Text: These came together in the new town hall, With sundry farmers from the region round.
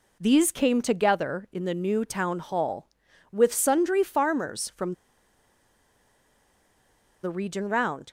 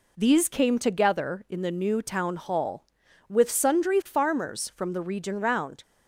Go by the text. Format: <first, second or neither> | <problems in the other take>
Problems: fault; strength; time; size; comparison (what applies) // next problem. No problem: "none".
second | pauses between "from" and "the"; strong; at 4.9 s; 2.3 s long